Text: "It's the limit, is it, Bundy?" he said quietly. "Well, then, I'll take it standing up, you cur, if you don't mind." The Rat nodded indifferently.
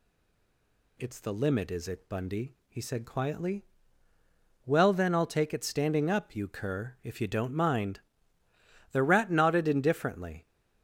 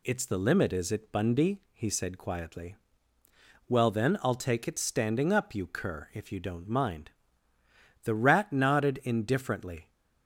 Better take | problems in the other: second | stays silent before the first word; until 0.9 s; 0.9 s long

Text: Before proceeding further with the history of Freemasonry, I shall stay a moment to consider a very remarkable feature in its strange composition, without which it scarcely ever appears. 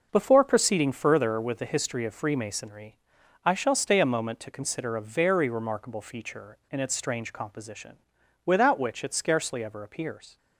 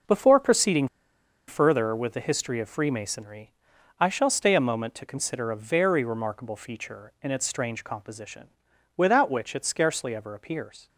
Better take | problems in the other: first | pauses between "proceeding" and "further"; noticeable; at 0.8 s; 0.60 s long

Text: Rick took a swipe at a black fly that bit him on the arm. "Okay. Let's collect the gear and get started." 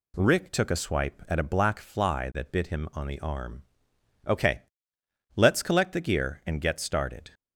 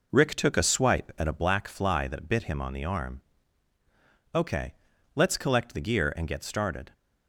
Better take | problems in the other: first | starts louder than the rest; noticeable; until 1.5 s; 4.5 dB

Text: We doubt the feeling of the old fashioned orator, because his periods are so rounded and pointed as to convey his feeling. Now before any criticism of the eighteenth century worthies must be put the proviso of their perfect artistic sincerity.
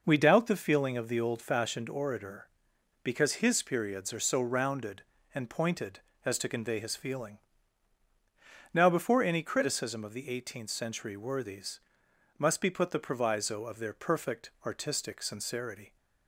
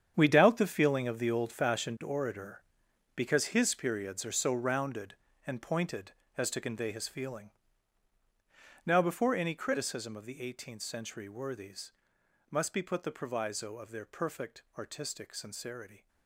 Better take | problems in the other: first | gets quieter; strong; throughout; 13 dB // pauses between "worthies" and "must"; noticeable; at 11.9 s; 0.58 s long; noticeable in the first

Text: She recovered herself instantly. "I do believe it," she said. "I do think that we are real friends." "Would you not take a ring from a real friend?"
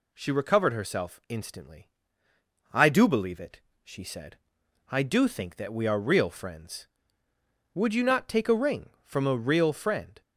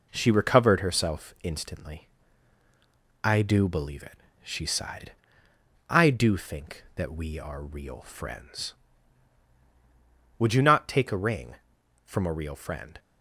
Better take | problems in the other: first | says "sighed" for "said"; at 4.6 s

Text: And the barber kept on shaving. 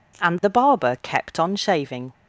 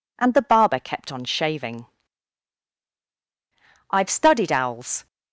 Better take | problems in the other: first | goes on to say "I've studied owls"; noticeable; from 3.8 s on; 1.1 s long

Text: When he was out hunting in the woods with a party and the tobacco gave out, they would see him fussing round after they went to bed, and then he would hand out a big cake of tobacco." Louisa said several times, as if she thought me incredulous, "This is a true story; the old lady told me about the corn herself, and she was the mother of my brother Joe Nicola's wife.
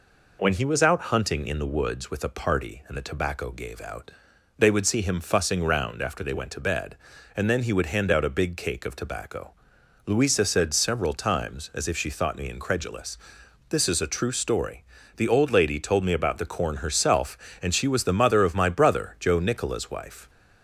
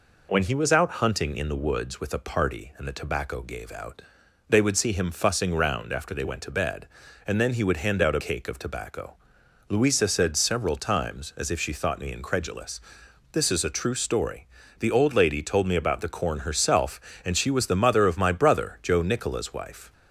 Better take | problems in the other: first | skips "big"; at 8.2 s

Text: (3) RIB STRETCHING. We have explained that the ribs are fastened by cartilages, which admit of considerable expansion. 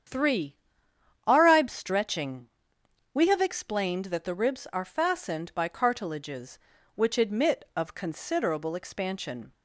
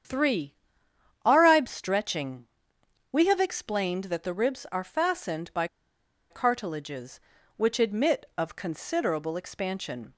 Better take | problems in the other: first | starts louder than the rest; strong; until 1.8 s; 8.5 dB; strong in the first // pauses between "by" and "cartilages"; noticeable; at 5.6 s; 0.64 s long

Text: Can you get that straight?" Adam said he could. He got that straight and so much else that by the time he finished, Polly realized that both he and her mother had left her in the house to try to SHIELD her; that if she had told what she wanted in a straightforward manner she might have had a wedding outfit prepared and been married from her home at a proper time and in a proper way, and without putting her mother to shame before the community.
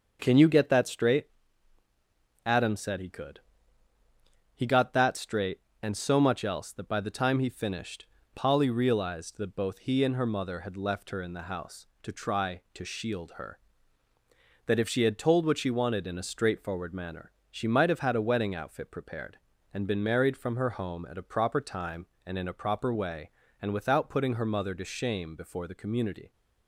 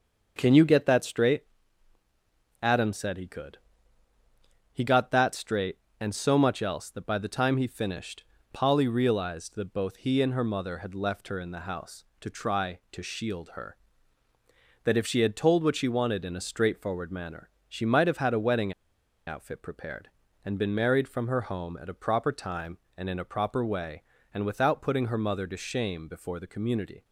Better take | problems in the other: first | starts louder than the rest; until 1.3 s; 6 dB; also in the first // pauses between "manner" and "she"; slight; at 17.4 s; 0.18 s long; slight in the first // pauses between "wedding" and "outfit"; noticeable; at 18.7 s; 0.55 s long

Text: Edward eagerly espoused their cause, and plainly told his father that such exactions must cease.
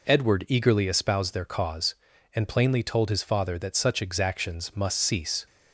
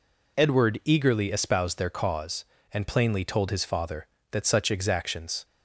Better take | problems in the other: first | stops before "must cease"; at 5.4 s

